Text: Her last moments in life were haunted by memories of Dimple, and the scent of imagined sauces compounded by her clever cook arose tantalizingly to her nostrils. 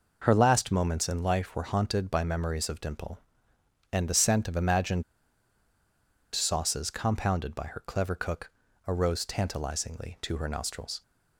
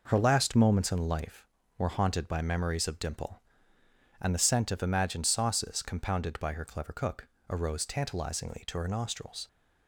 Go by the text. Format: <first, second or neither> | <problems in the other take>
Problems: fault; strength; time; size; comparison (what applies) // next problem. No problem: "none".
second | pauses between "imagined" and "sauces"; strong; at 5.0 s; 1.3 s long // pauses between "cook" and "arose"; at 8.4 s; 0.38 s long; slight in the second